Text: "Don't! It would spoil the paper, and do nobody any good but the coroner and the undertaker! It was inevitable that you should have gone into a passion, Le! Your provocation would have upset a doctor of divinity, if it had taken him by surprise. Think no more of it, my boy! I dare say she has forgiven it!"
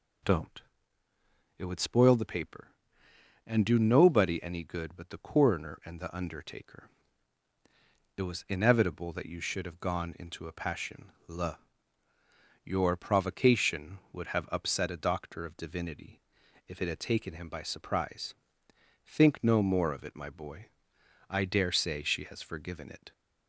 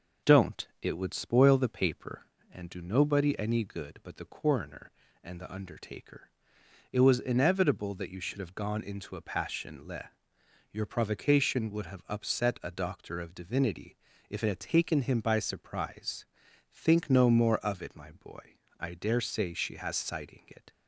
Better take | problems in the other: first | says "sighting" for "forgiven"; at 19.9 s

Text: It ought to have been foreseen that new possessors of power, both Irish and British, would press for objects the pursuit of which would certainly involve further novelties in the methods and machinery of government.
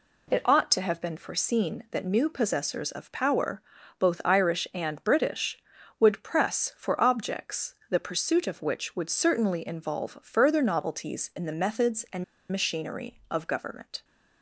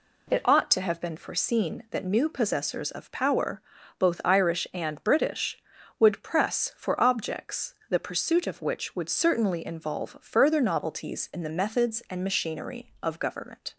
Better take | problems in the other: second | pauses between "and" and "machinery"; slight; at 12.2 s; 0.27 s long

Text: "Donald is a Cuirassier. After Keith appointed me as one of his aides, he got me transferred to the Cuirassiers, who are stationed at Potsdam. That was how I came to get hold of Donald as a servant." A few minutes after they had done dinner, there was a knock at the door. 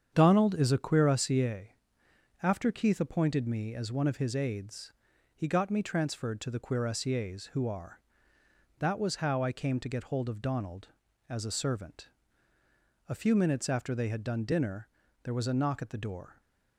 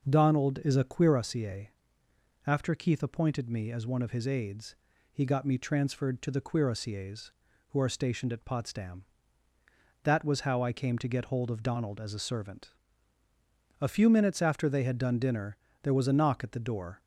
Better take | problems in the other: second | starts louder than the rest; strong; until 1.1 s; 8 dB; also in the second // skips "stationed at Potsdam"; at 8.3 s

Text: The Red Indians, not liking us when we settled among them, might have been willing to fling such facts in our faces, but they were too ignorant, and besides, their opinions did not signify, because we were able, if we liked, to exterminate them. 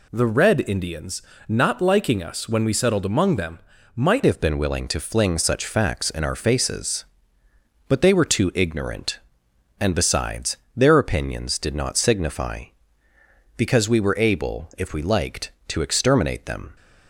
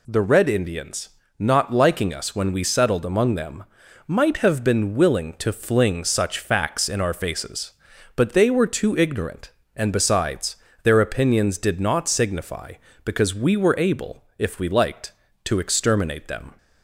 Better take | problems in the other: second | changes voice at "have"; from 4.2 s on; 12.5 s long

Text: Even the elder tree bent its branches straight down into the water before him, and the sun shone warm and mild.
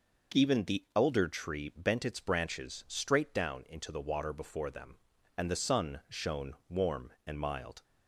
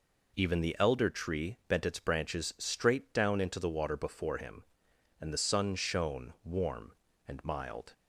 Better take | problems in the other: second | says "them" for "him"; at 4.7 s

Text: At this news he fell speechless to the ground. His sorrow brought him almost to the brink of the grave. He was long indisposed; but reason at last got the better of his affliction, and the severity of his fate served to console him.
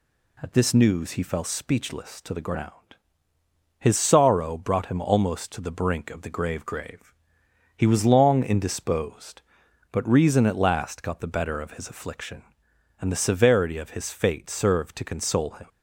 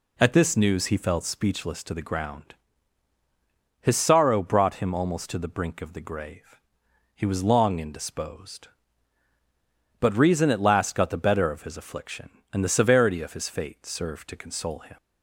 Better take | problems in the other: second | says "grave" twice; at 6.6 s

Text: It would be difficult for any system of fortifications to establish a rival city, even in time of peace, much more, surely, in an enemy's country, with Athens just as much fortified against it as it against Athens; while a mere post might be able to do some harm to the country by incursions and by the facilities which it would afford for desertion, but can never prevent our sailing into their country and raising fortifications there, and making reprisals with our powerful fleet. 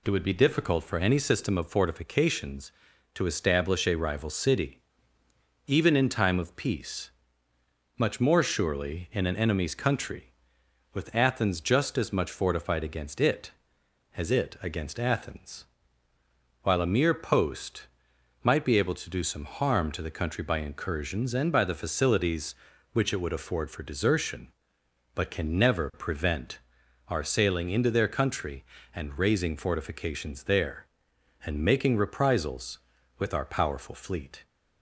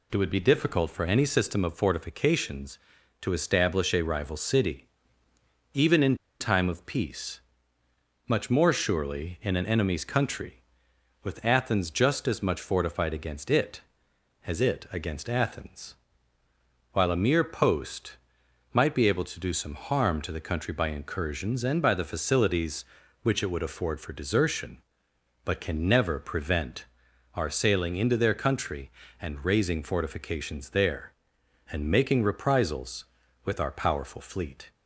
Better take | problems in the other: first | pauses between "in" and "time"; slight; at 6.1 s; 0.24 s long // pauses between "post" and "might"; noticeable; at 18.1 s; 0.56 s long; noticeable in the first // pauses between "prevent" and "our"; noticeable; at 26.8 s; 0.50 s long; noticeable in the first

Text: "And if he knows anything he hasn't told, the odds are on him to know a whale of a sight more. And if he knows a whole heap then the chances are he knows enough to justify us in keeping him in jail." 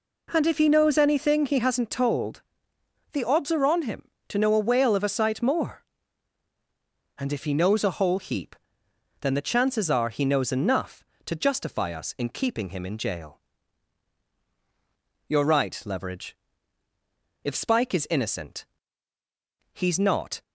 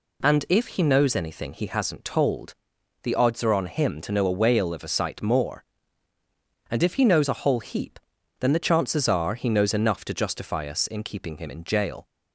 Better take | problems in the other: second | pauses between "heap" and "then"; noticeable; at 8.5 s; 0.68 s long; also in the second // goes on to say "You're right Leverage If Spike is innocent he's not"; strong; from 15.2 s on; 5.1 s long

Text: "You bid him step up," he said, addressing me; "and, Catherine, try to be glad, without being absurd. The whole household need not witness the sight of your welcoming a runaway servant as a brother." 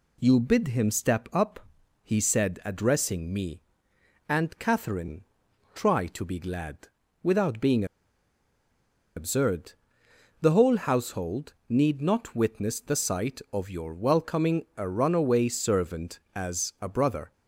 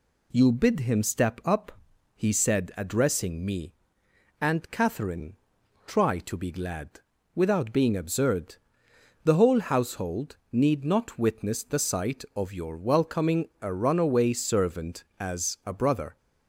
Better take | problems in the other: second | pauses between "being" and "absurd"; strong; at 7.8 s; 1.3 s long

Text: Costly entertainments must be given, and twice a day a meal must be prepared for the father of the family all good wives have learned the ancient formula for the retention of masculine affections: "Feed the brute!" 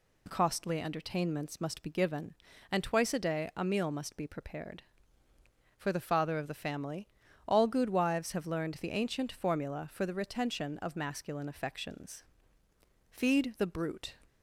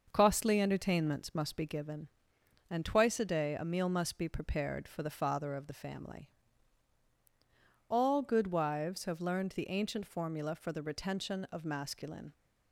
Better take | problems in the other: first | starts louder than the rest; until 1.1 s; 6 dB // pauses between "family" and "all"; strong; at 6.2 s; 1.6 s long; also in the first // stops before "affections Feed the brute"; at 12.3 s

